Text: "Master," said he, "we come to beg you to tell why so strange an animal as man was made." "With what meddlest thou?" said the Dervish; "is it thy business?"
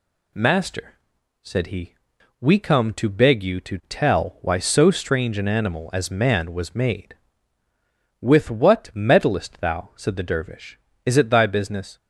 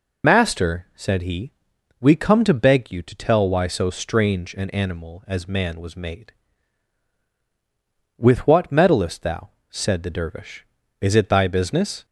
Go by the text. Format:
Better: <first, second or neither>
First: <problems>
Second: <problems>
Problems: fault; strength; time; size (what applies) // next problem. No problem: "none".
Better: first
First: none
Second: loses the start of "Master"; at 0.2 s; 65 ms